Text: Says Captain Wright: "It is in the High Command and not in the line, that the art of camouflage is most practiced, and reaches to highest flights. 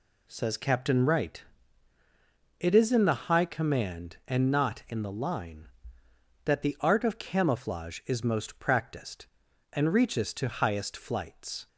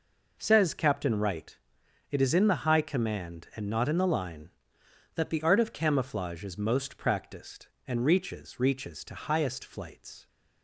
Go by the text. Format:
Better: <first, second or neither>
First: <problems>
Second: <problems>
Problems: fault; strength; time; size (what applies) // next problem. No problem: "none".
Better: first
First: none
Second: says "reaches" twice; at 8.5 s